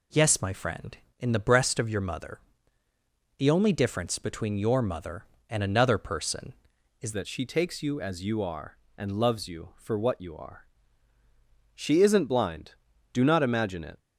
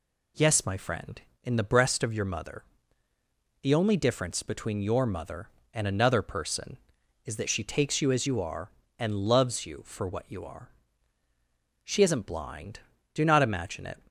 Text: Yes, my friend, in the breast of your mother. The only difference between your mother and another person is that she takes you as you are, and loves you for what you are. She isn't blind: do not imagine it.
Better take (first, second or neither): second